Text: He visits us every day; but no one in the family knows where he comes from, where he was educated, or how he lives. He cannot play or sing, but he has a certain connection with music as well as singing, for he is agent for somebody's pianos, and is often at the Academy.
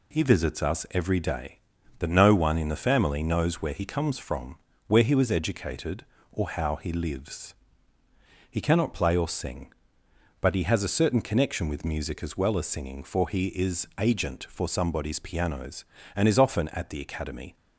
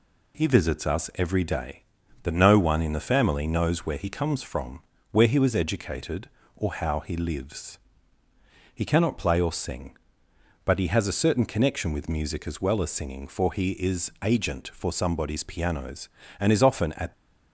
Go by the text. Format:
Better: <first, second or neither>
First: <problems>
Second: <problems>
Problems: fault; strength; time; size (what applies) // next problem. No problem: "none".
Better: first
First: none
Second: stops before "the Academy"; at 17.1 s